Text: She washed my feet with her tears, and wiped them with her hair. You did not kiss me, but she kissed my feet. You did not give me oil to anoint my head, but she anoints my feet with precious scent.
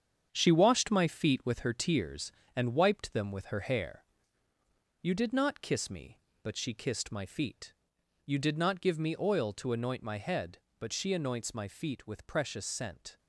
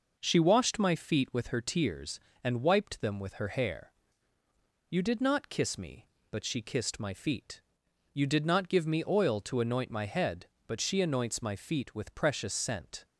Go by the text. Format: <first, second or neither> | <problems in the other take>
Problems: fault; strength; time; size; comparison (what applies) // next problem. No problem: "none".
second | gets quieter; strong; throughout; 7.5 dB